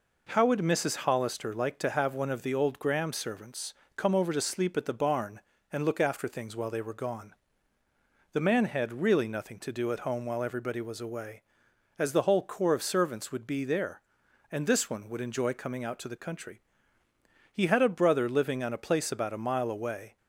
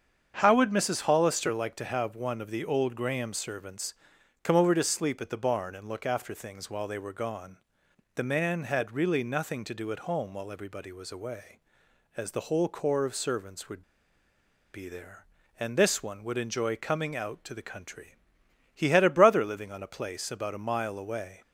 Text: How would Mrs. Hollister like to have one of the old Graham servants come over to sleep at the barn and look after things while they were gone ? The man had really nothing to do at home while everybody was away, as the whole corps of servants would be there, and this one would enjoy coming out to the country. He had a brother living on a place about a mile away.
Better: first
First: pauses between "servants" and "come"; slight; at 3.7 s; 0.24 s long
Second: starts louder than the rest; strong; until 1.4 s; 7.5 dB // pauses between "servants" and "come"; noticeable; at 3.9 s; 0.50 s long // pauses between "would" and "be"; noticeable; at 13.8 s; 0.93 s long

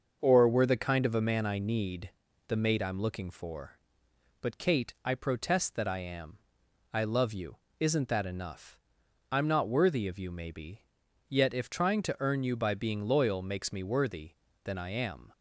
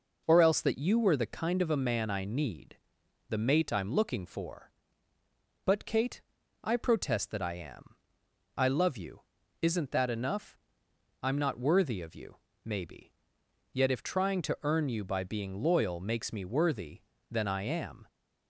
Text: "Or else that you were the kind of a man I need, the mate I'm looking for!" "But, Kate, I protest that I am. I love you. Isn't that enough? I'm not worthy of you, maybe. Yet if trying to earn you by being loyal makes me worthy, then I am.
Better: second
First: starts louder than the rest; until 1.2 s; 6.5 dB // skips "else that you"; at 0.4 s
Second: none

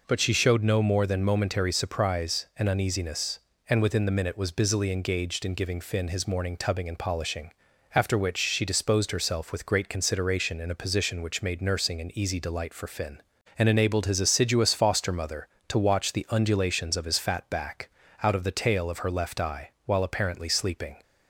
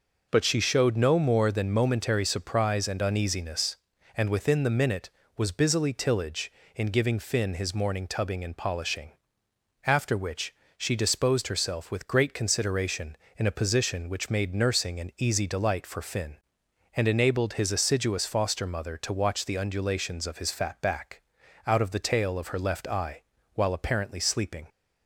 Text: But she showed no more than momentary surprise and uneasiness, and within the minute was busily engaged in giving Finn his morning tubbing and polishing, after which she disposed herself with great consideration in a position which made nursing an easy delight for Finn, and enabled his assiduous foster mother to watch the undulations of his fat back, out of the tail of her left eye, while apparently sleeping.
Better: first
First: none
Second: says "tillage" for "engaged"; at 5.9 s // pauses between "which" and "she"; slight; at 10.5 s; 0.22 s long

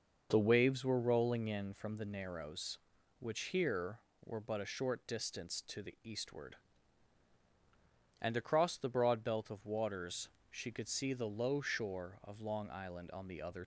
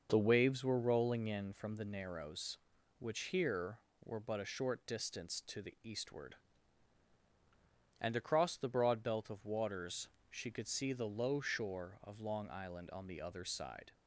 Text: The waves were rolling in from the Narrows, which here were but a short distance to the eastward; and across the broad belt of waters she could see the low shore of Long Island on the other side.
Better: second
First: pauses between "waters" and "she"; slight; at 10.2 s; 0.20 s long // stops before "side"; at 13.6 s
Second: pauses between "waters" and "she"; slight; at 10.0 s; 0.20 s long

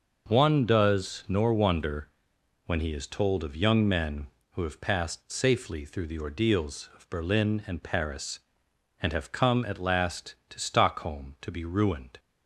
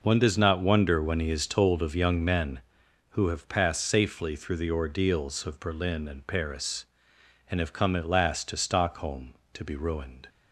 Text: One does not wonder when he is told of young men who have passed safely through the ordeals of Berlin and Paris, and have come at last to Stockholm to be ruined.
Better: second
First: starts louder than the rest; noticeable; until 1.3 s; 6 dB // says "nor" for "not"; at 1.2 s // pauses between "wonder" and "when"; noticeable; at 2.0 s; 0.56 s long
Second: none

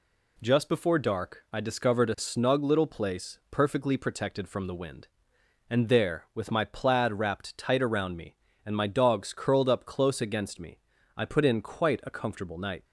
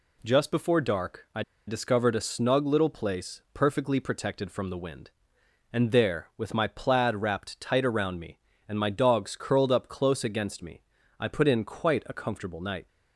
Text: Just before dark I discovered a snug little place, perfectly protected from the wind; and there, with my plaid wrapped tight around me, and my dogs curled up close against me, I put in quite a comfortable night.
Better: first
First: none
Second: pauses between "I" and "discovered"; slight; at 1.4 s; 0.25 s long

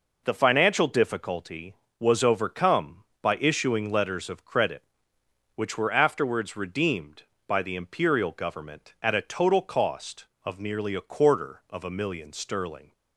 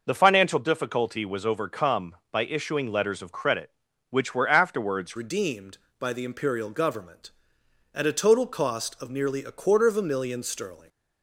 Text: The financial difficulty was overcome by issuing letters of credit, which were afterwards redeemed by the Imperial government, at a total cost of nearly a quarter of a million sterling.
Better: first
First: none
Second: changes voice at "redeemed"; from 5.1 s on; 5.7 s long

